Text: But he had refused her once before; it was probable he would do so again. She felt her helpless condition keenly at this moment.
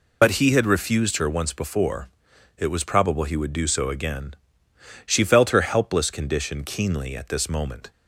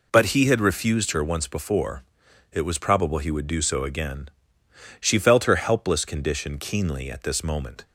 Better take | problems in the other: second | loses the start of "But"; at 0.2 s; 55 ms

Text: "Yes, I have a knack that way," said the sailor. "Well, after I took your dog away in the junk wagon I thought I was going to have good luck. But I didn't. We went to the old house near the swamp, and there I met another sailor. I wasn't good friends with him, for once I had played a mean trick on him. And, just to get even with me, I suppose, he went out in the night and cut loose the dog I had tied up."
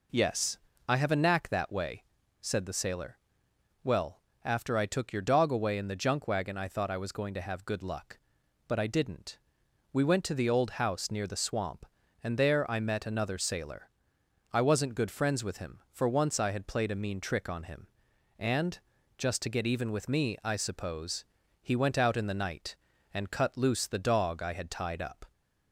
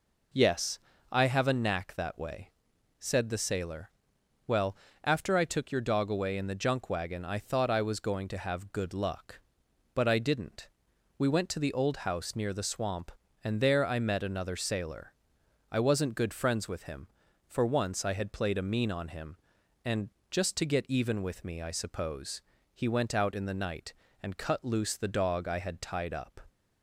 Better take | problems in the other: first | skips "trick"; at 18.9 s

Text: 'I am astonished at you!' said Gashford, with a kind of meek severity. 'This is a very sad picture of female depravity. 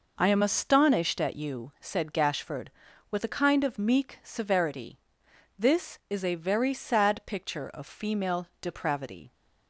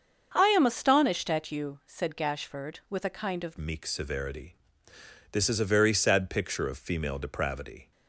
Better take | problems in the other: first | starts louder than the rest; until 1.3 s; 7 dB // changes voice at "meek"; from 3.5 s on; 4.4 s long

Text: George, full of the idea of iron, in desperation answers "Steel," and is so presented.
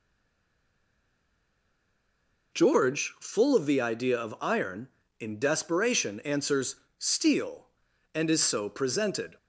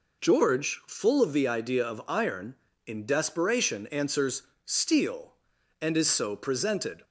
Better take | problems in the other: second | stays silent before the first word; strong; until 2.5 s; 2.5 s long // pauses between "answers" and "Steel"; slight; at 6.7 s; 0.24 s long; slight in the second

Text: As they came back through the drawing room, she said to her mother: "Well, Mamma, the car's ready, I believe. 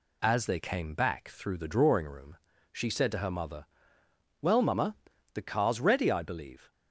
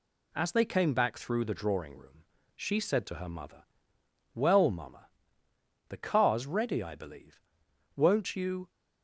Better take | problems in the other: first | goes on to say "Won't you"; noticeable; from 7.9 s on; 0.74 s long

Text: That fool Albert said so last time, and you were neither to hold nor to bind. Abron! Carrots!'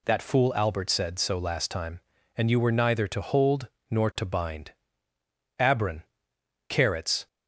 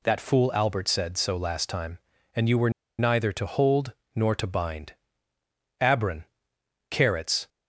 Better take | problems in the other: first | pauses between "were" and "neither"; slight; at 2.6 s; 0.28 s long // pauses between "hold" and "nor"; slight; at 3.9 s; 0.22 s long; slight in the first

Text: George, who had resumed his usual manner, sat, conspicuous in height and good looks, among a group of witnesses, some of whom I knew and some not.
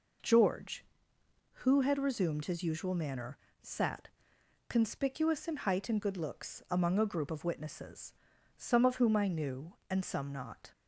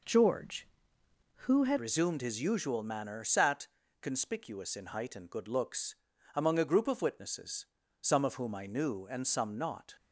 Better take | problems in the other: first | changes voice at "resumed"; from 1.7 s on; 8.2 s long

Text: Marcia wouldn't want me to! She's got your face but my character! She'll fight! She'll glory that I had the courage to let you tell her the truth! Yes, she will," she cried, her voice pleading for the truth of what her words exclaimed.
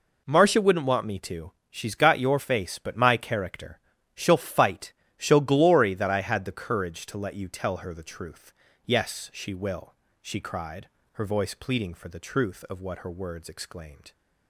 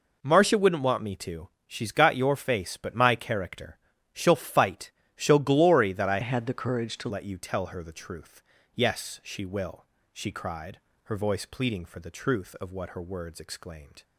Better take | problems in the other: first | changes voice from "had" to "to"; from 6.2 to 7.0 s; 0.8 s long

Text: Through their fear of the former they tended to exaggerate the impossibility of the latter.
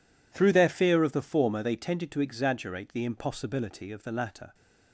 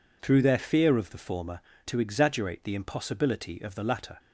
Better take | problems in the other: first | skips "they tended"; at 1.7 s

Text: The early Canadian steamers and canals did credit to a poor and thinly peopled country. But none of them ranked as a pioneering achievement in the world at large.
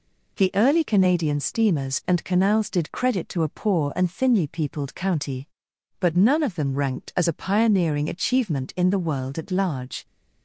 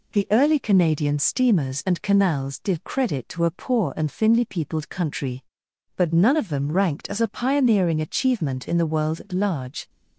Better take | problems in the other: second | says "county" for "country"; at 4.9 s

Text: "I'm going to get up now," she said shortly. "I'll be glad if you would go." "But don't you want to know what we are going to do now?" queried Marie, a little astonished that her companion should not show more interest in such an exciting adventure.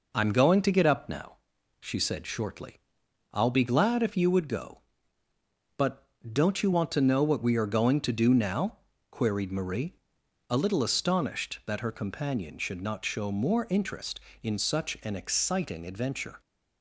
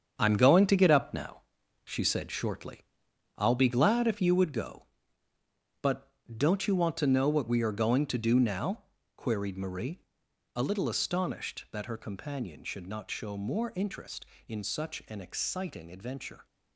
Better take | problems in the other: first | gets quieter; strong; throughout; 9 dB // pauses between "But" and "don't"; slight; at 6.0 s; 0.30 s long; slight in the first

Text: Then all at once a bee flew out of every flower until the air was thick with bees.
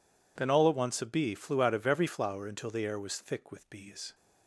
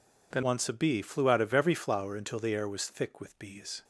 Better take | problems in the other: first | skips "all at"; at 0.4 s

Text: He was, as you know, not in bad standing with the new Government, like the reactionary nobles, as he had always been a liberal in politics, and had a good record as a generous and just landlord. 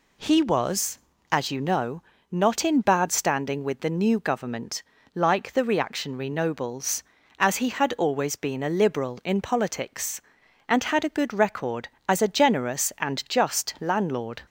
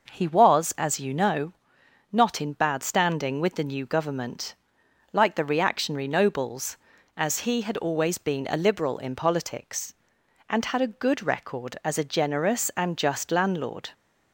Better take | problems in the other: neither | none

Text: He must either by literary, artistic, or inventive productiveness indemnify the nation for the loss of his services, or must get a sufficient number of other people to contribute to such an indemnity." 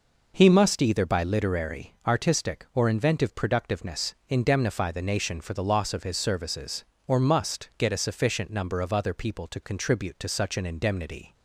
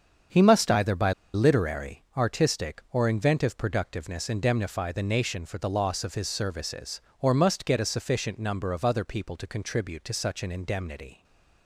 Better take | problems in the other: first | starts louder than the rest; strong; until 1.5 s; 7 dB // pauses between "by" and "literary"; slight; at 1.1 s; 0.22 s long // stays silent after the last word; slight; from 11.1 s on; 0.5 s long

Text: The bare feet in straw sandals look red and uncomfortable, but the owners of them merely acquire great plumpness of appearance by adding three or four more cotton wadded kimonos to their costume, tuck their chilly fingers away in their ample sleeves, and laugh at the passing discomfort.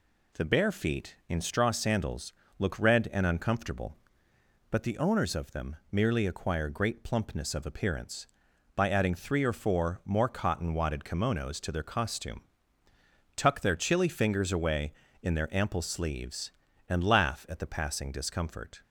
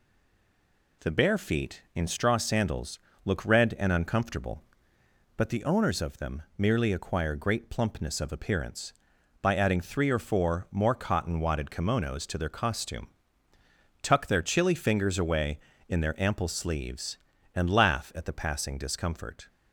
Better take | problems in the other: first | stays silent before the first word; until 1.0 s; 1.0 s long // pauses between "sandals" and "look"; slight; at 2.9 s; 0.26 s long; slight in the first // pauses between "them" and "merely"; slight; at 6.4 s; 0.16 s long; slight in the first

